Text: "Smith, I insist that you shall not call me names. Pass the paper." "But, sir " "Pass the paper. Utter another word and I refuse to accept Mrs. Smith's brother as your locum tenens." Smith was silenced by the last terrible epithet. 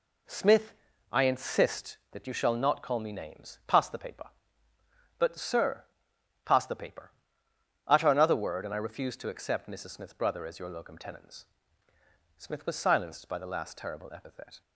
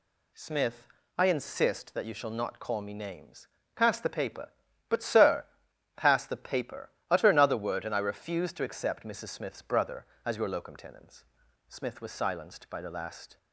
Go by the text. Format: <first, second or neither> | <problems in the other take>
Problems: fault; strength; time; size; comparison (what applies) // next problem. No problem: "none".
first | stops before "terrible epithet"; at 13.3 s